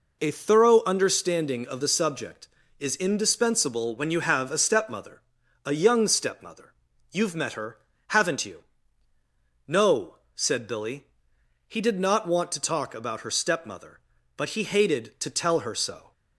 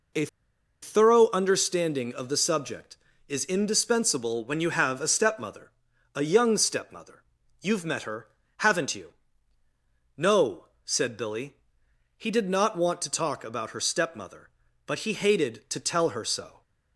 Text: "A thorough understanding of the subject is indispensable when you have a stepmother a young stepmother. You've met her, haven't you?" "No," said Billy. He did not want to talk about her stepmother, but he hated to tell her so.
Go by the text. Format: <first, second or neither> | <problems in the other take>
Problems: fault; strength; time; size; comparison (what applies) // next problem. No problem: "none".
first | pauses between "A" and "thorough"; noticeable; at 0.2 s; 0.57 s long // pauses between "stepmother" and "a"; noticeable; at 5.6 s; 0.46 s long; noticeable in the first